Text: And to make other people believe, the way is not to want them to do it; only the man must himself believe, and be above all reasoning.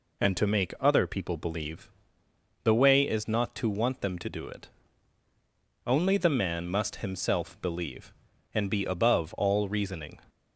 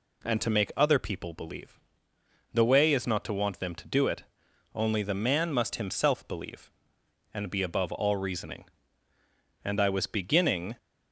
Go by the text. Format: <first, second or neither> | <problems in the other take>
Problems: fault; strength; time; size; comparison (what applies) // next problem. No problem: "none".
first | goes on to say "And I was beginning"; noticeable; from 9.6 s on; 1.1 s long